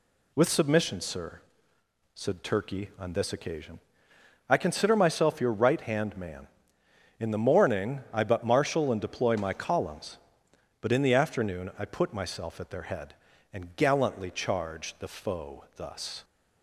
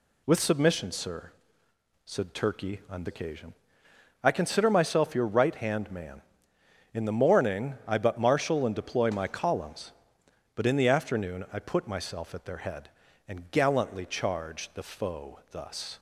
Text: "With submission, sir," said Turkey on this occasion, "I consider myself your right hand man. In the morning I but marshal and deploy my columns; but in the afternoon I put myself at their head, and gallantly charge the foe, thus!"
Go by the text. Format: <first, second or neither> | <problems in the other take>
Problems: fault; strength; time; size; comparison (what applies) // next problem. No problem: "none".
first | skips "this"; at 3.0 s